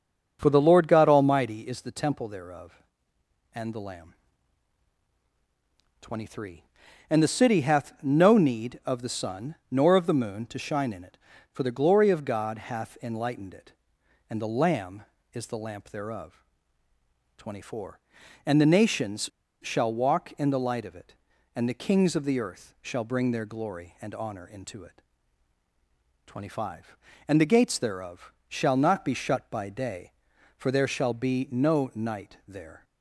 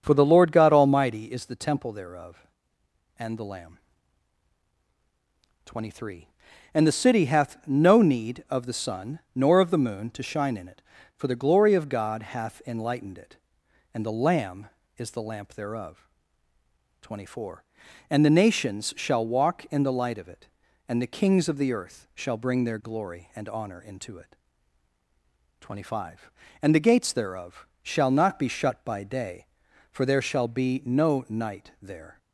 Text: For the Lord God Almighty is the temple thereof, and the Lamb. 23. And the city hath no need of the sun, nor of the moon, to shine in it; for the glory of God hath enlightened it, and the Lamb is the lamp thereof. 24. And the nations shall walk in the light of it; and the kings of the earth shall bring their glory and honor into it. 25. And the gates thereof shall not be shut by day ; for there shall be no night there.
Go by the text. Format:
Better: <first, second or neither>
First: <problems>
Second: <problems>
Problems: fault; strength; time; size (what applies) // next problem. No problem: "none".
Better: second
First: starts louder than the rest; until 1.4 s; 6.5 dB // pauses between "nations" and "shall"; at 19.2 s; 0.37 s long // pauses between "thereof" and "shall"; slight; at 28.3 s; 0.16 s long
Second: starts louder than the rest; until 1.0 s; 6.5 dB // pauses between "thereof" and "shall"; slight; at 27.6 s; 0.16 s long